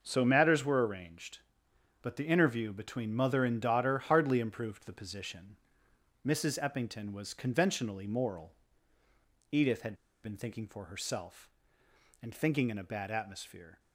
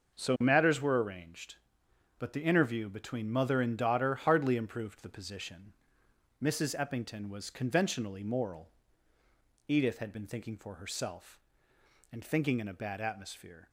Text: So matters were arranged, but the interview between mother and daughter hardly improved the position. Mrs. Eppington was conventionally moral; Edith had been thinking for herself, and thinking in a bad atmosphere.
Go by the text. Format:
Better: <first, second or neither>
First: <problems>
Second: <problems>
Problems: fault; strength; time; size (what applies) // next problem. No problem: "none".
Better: second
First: pauses between "had" and "been"; slight; at 9.9 s; 0.28 s long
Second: none